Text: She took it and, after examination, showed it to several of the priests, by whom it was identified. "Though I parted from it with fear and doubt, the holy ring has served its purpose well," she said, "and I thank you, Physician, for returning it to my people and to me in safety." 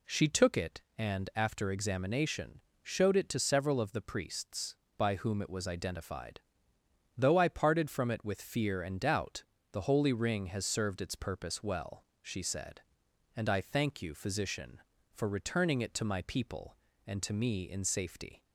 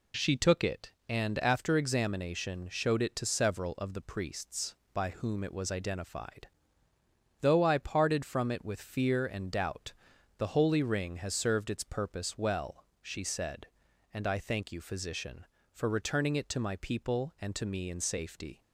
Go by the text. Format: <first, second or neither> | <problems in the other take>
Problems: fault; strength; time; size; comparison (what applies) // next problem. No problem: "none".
neither | none